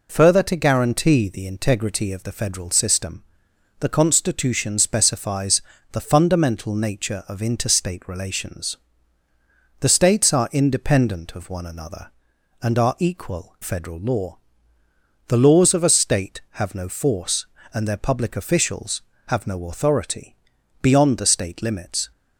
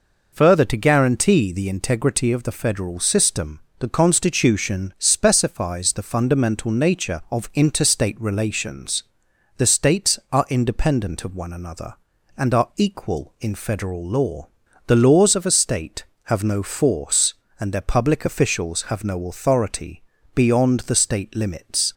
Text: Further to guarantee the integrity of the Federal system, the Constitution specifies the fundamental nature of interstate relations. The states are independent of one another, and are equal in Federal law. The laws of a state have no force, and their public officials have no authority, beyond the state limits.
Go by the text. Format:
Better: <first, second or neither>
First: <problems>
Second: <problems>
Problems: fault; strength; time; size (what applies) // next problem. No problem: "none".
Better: second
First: pauses between "specifies" and "the"; slight; at 5.6 s; 0.32 s long // skips "in"; at 13.5 s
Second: none